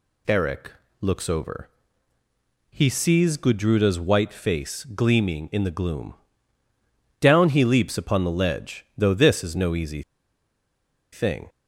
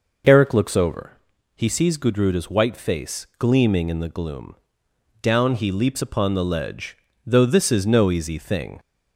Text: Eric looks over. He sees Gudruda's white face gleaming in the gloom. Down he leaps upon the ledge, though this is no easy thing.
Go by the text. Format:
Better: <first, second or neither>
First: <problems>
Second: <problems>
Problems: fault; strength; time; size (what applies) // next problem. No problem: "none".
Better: second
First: pauses between "Eric" and "looks"; slight; at 0.7 s; 0.30 s long // pauses between "easy" and "thing"; at 10.0 s; 1.1 s long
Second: none